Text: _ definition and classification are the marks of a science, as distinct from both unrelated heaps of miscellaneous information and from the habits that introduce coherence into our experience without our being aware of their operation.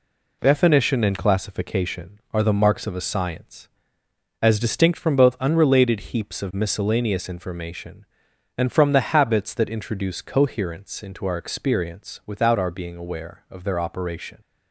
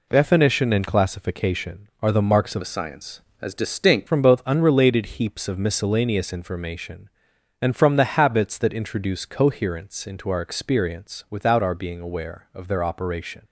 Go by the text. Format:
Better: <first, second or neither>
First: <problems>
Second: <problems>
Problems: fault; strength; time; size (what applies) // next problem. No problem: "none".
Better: first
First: none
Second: changes voice from "a" to "distinct"; from 2.6 to 4.0 s; 1.4 s long